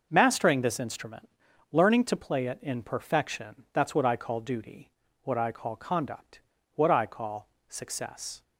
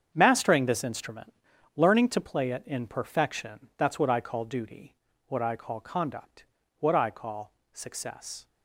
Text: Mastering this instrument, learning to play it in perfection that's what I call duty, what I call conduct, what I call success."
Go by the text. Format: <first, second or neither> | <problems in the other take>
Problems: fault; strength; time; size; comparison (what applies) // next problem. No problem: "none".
first | gets quieter; strong; throughout; 12 dB // pauses between "call" and "success"; slight; at 7.5 s; 0.20 s long; slight in the first